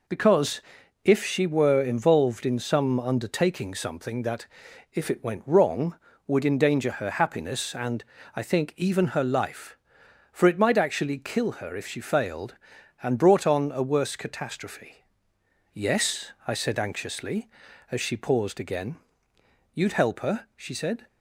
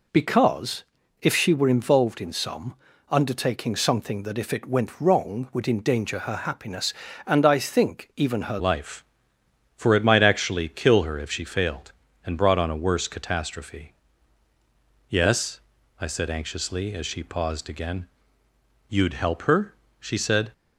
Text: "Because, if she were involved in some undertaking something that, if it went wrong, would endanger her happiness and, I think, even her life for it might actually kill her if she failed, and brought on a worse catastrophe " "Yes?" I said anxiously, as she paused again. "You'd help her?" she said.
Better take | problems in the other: first | pauses between "some" and "undertaking"; slight; at 2.7 s; 0.36 s long // changes voice at "life"; from 8.5 s on; 12.0 s long

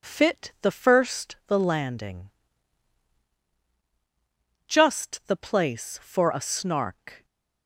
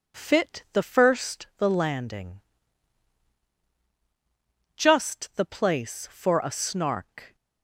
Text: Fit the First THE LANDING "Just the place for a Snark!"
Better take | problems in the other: neither | pauses between "LANDING" and "Just"; strong; the same in both

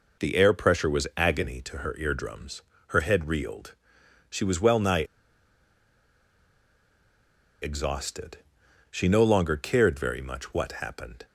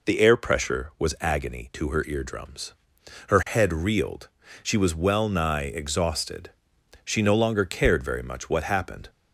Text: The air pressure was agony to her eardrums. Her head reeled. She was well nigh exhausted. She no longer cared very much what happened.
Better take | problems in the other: second | pauses between "nigh" and "exhausted"; strong; at 5.0 s; 2.5 s long

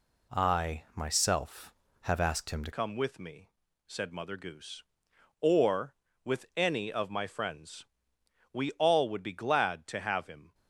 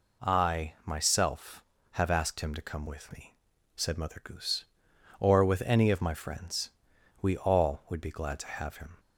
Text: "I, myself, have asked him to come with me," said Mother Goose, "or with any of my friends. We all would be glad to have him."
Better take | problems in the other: second | changes voice at "come"; from 2.7 s on; 7.8 s long

